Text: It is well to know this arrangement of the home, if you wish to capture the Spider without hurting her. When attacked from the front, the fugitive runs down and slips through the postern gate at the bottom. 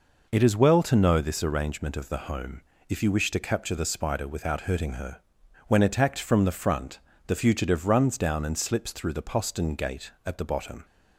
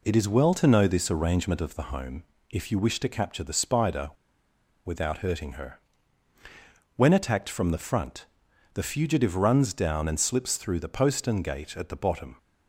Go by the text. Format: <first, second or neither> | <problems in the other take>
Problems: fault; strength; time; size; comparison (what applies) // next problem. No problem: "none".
first | pauses between "Spider" and "without"; noticeable; at 4.0 s; 0.75 s long